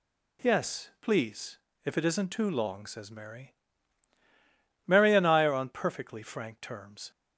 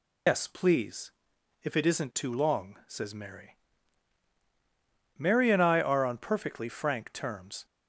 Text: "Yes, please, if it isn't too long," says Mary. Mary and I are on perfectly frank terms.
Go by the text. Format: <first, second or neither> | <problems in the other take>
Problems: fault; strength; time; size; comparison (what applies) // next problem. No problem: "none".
first | loses the start of "Yes"; at 0.2 s; 120 ms